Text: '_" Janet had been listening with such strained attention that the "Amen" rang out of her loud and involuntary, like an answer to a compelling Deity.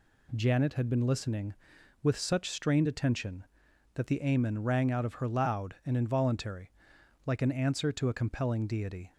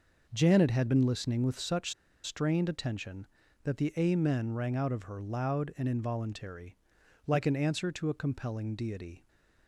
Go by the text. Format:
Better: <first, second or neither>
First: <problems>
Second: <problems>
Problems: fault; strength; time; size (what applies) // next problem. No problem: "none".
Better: first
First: none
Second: pauses between "such" and "strained"; slight; at 1.9 s; 0.30 s long